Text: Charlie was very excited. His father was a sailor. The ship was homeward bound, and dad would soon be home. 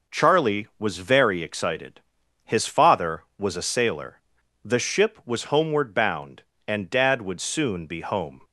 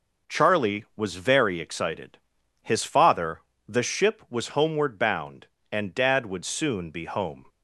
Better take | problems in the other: first | skips "was a sailor"; at 3.5 s

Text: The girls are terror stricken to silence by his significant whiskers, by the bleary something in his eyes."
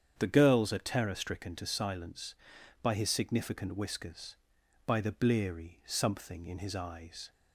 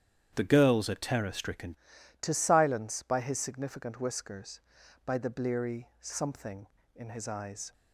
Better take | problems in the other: first | starts louder than the rest; strong; until 1.3 s; 9.5 dB; strong in the first // changes voice at "to"; from 2.2 s on; 5.5 s long

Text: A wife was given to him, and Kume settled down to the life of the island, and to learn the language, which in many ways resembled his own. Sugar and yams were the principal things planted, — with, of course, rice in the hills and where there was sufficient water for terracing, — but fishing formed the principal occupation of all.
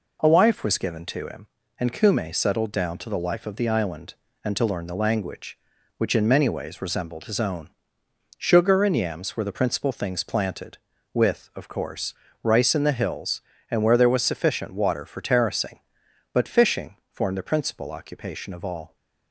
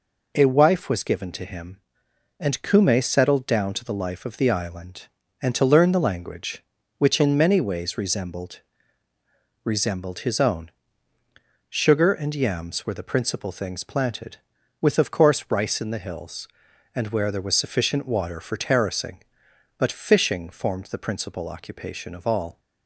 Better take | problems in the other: first | says "resembled" twice; at 9.6 s

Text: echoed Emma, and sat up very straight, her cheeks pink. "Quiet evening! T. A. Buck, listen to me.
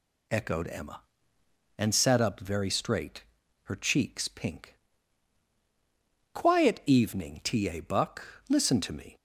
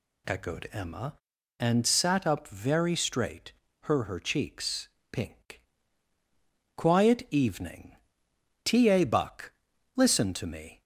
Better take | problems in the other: first | says "her" twice; at 4.0 s // pauses between "cheeks" and "pink"; slight; at 4.8 s; 0.24 s long

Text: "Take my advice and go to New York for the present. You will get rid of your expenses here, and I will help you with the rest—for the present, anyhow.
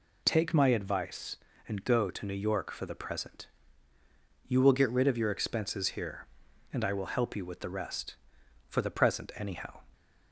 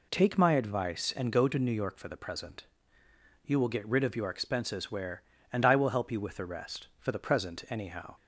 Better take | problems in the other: first | says "where" for "here"; at 4.8 s

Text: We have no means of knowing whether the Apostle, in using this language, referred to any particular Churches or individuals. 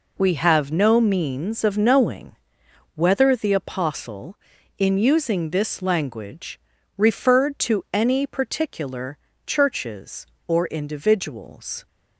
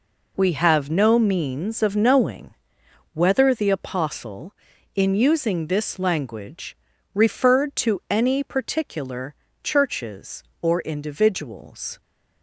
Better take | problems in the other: neither | pauses between "knowing" and "whether"; noticeable; the same in both // pauses between "particular" and "Churches"; slight; the same in both

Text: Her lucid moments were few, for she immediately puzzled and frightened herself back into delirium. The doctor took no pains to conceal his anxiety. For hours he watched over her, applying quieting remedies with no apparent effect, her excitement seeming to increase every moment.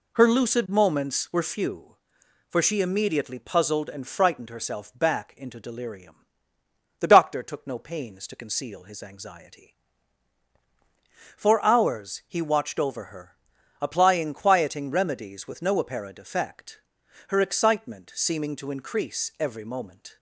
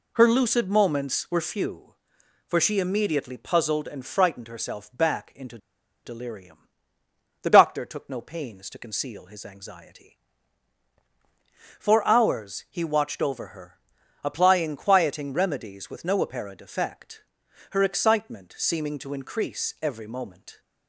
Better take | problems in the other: first | pauses between "into" and "delirium"; noticeable; at 5.5 s; 0.47 s long

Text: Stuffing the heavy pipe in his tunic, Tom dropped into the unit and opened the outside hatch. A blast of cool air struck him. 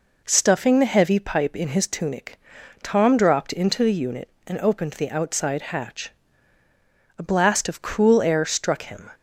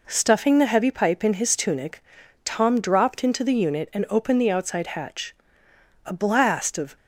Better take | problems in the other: first | stops before "cool air struck him"; at 6.9 s

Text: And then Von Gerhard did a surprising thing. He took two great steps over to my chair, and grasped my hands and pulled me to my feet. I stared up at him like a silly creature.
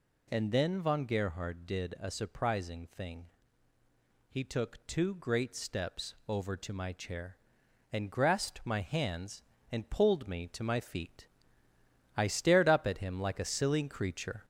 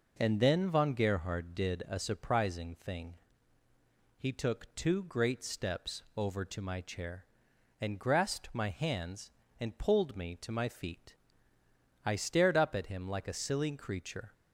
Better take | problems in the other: second | gets louder; slight; throughout; 2.5 dB

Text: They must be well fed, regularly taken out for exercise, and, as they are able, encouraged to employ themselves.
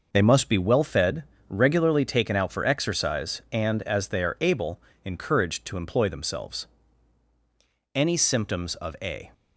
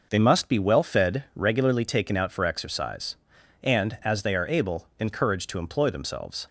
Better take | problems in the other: second | goes on to say "Any symptoms of a"; from 7.9 s on; 1.3 s long

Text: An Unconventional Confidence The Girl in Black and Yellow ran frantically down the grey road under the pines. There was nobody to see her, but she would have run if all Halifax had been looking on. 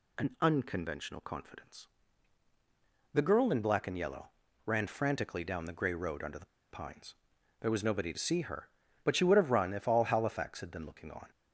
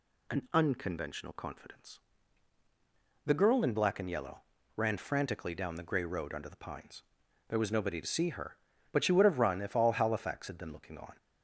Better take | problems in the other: second | pauses between "Confidence" and "The"; at 1.8 s; 1.2 s long; also in the second // pauses between "Yellow" and "ran"; slight; at 4.2 s; 0.36 s long; slight in the second // pauses between "the" and "pines"; slight; at 6.4 s; 0.24 s long

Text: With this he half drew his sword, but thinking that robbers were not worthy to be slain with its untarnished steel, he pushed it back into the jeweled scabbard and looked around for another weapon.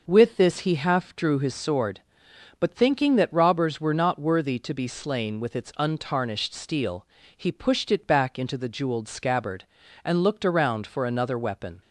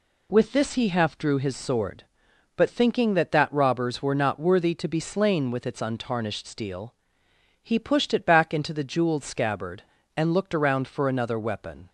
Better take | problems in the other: first | says "that" twice; at 3.3 s

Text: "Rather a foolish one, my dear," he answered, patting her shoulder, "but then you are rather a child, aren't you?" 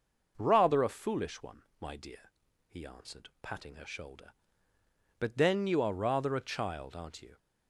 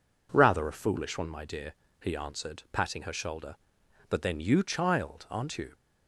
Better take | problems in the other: first | skips "are rather a"; at 4.6 s

